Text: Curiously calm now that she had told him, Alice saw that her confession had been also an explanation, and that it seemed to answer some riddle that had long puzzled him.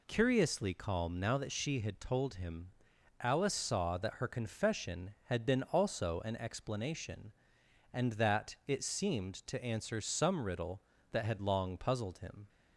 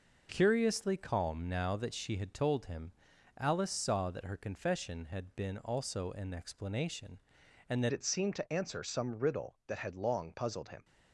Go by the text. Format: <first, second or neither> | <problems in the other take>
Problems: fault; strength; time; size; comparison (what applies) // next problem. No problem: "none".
first | changes voice at "it"; from 7.9 s on; 2.9 s long